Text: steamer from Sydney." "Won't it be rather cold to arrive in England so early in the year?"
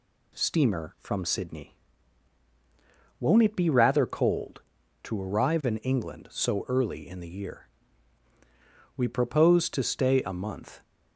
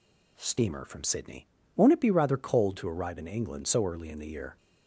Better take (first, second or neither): second